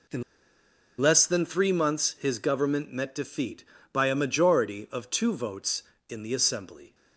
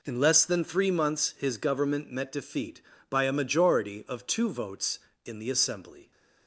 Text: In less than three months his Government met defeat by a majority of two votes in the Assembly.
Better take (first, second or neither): second